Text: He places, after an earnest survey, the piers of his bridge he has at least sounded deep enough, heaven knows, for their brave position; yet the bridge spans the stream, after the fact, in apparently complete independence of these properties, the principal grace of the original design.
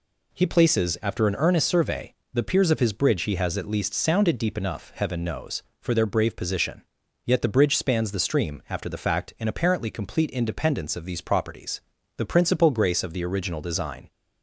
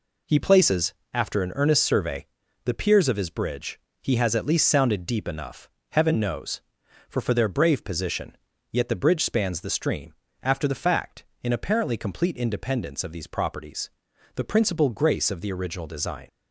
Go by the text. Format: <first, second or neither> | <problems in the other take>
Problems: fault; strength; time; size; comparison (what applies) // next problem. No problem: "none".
first | pauses between "bridge" and "he"; slight; at 3.7 s; 0.22 s long // says "for" twice; at 7.2 s